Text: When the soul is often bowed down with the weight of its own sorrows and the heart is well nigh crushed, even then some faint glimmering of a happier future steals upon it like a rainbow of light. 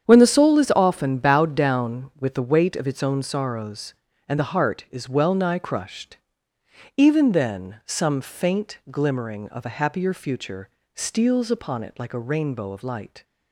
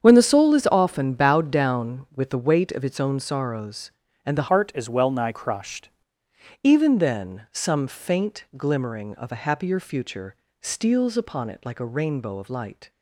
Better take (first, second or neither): first